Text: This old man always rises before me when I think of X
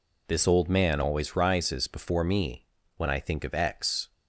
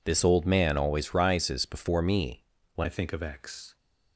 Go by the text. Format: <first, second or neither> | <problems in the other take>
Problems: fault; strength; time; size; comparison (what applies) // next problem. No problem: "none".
first | pauses between "me" and "when"; slight; at 2.4 s; 0.30 s long; slight in the first // changes voice at "I"; from 2.8 s on; 0.9 s long